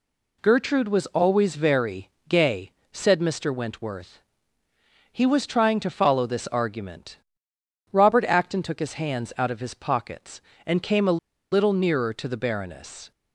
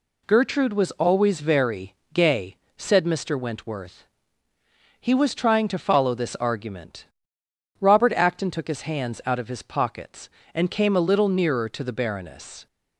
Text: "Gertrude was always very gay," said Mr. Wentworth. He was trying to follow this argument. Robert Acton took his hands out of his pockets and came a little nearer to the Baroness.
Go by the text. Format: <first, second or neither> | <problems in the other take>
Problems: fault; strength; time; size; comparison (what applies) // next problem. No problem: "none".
second | pauses between "very" and "gay"; slight; at 2.1 s; 0.18 s long; slight in the second // pauses between "a" and "little"; slight; at 11.1 s; 0.33 s long